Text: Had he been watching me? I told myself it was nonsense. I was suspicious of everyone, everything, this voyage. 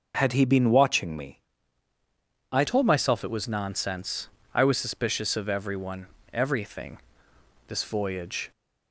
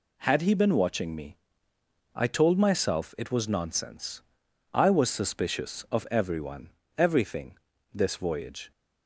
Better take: second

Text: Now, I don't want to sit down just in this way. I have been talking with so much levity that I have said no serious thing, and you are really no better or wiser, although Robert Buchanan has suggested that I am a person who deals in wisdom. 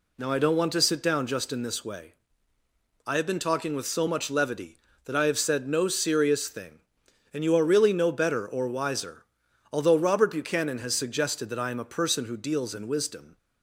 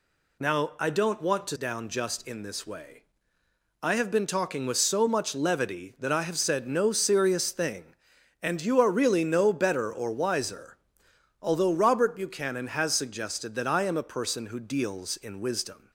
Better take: first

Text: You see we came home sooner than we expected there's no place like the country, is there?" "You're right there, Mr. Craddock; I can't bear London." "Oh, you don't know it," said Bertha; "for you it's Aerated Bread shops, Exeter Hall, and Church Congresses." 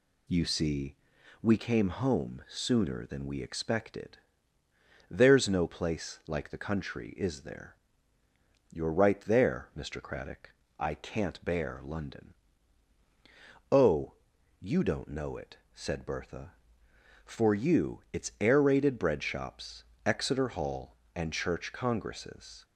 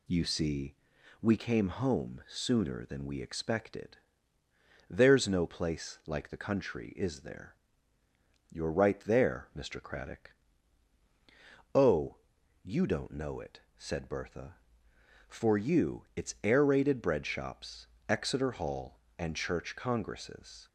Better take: first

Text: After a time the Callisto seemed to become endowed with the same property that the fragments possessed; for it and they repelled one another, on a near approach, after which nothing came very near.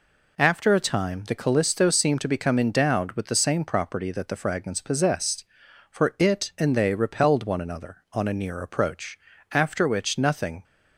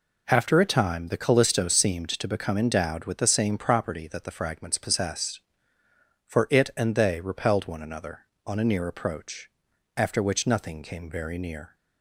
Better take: second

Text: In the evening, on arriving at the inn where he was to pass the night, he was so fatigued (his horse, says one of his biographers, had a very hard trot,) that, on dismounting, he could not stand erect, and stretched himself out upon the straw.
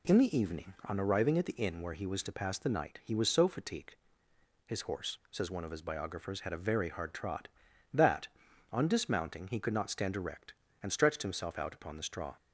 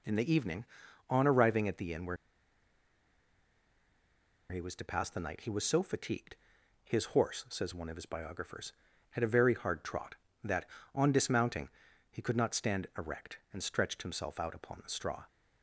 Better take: first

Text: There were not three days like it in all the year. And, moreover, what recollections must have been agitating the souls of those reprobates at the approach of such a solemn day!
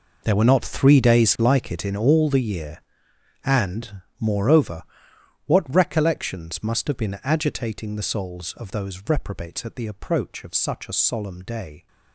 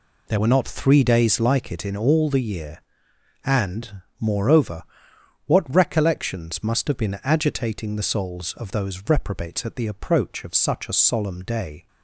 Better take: second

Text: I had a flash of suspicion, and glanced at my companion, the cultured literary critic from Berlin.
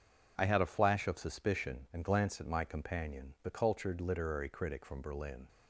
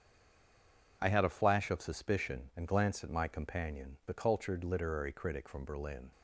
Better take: first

